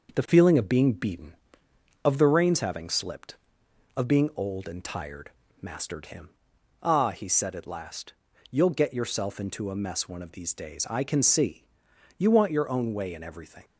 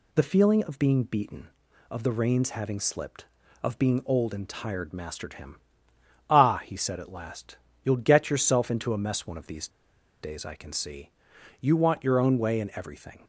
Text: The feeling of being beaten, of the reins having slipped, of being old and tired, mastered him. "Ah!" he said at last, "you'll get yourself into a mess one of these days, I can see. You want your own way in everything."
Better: first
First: none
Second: pauses between "these" and "days"; noticeable; at 9.6 s; 0.52 s long

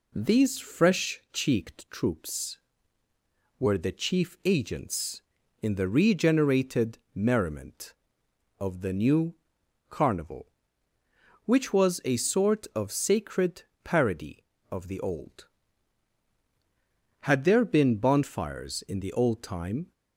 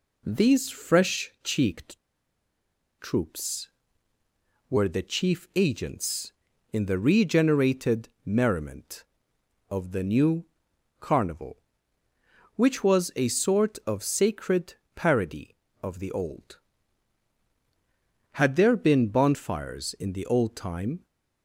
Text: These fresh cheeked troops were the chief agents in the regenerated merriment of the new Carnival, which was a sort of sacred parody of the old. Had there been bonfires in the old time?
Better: first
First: pauses between "regenerated" and "merriment"; slight; at 6.9 s; 0.16 s long // pauses between "new" and "Carnival"; noticeable; at 9.3 s; 0.54 s long // pauses between "sacred" and "parody"; slight; at 13.6 s; 0.24 s long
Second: pauses between "cheeked" and "troops"; at 1.9 s; 1.0 s long // pauses between "regenerated" and "merriment"; slight; at 8.0 s; 0.16 s long // pauses between "new" and "Carnival"; noticeable; at 10.4 s; 0.54 s long // pauses between "sacred" and "parody"; slight; at 14.7 s; 0.24 s long

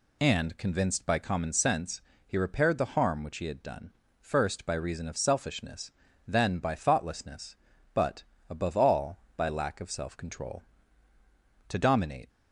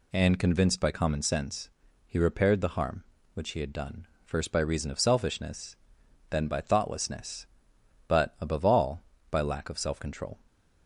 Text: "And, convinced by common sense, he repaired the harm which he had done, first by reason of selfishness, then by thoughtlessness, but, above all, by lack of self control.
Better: second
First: goes on to say "To dominate"; noticeable; from 11.6 s on; 0.62 s long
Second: none

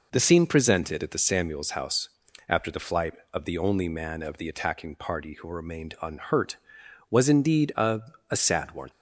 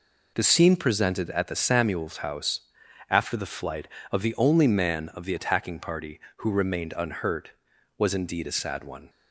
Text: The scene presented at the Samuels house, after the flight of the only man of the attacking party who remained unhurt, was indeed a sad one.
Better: second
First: says "a" twice; at 8.2 s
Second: none

